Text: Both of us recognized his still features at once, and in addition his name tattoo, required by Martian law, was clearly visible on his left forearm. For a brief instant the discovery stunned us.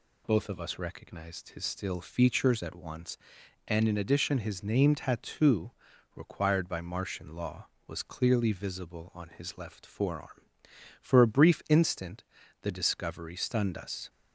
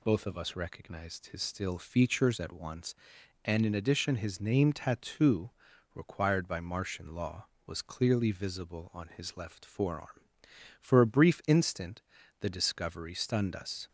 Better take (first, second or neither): neither